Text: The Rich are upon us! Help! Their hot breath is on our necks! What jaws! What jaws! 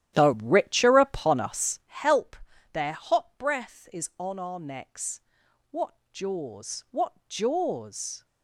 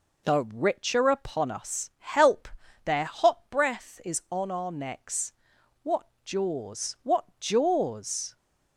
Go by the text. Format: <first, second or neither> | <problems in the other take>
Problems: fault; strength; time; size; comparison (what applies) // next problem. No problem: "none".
second | starts louder than the rest; strong; until 2.0 s; 12 dB // pauses between "What" and "jaws"; slight; at 5.9 s; 0.18 s long; slight in the second // pauses between "What" and "jaws"; slight; at 7.1 s; 0.16 s long; slight in the second